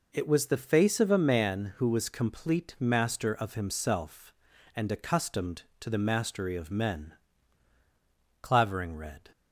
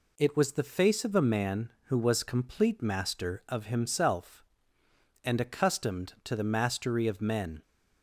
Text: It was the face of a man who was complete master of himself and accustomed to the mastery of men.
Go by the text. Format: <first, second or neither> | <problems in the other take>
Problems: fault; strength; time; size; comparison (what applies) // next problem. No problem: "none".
second | goes on to say "Clavering read"; noticeable; from 8.4 s on; 0.88 s long